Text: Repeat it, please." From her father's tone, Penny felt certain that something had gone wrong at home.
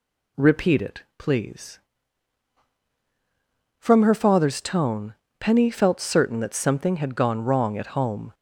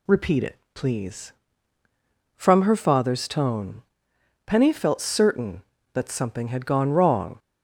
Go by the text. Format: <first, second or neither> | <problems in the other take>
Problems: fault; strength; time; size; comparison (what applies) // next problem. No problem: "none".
first | stops before "at home"; at 7.3 s